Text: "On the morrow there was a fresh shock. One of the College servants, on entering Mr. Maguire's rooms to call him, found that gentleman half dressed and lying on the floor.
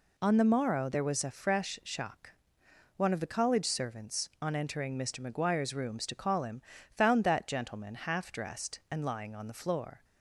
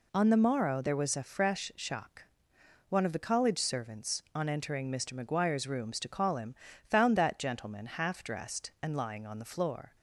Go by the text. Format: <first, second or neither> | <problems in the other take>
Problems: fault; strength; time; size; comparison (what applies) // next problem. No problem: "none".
neither | none